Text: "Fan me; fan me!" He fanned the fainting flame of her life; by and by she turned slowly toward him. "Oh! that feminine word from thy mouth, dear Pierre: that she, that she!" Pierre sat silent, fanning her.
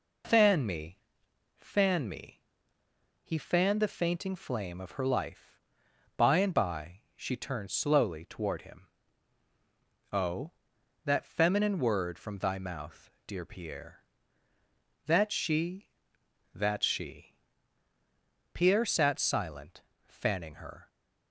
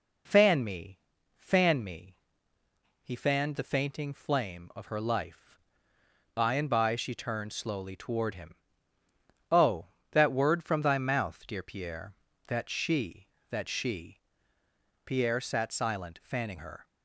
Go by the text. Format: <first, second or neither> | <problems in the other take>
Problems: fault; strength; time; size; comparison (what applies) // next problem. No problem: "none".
first | skips "feminine"; at 10.3 s